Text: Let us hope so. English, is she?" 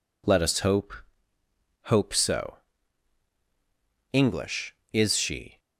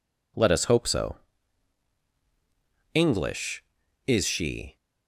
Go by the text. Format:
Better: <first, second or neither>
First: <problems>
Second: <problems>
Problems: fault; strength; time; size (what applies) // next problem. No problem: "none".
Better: second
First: says "hope" twice; at 1.8 s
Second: none